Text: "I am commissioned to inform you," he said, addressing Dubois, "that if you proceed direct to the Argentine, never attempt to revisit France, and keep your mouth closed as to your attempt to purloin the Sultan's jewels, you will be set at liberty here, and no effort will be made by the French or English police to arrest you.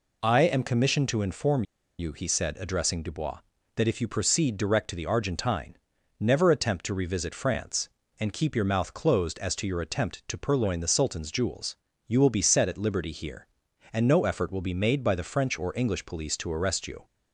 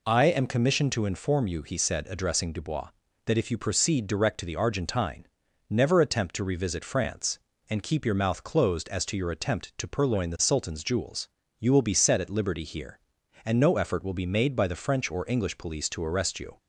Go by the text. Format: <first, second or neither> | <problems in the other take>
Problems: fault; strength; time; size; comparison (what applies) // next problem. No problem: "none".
second | pauses between "inform" and "you"; slight; at 1.6 s; 0.35 s long